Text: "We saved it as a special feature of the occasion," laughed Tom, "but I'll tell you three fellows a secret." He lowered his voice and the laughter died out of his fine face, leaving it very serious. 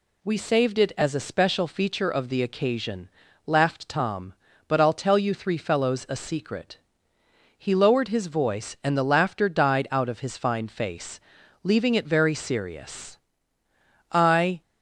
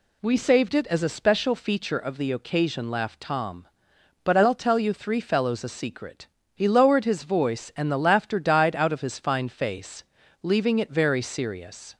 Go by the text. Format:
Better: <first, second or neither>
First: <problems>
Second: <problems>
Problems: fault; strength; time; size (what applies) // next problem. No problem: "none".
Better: second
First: goes on to say "I"; from 14.1 s on; 0.50 s long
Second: none